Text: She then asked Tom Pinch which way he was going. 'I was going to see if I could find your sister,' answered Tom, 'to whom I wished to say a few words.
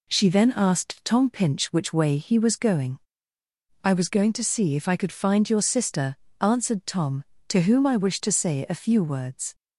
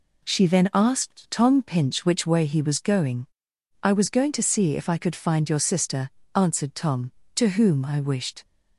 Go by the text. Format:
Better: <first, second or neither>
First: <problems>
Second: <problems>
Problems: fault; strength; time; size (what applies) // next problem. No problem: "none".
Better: first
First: none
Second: stops before "to say a few words"; at 8.4 s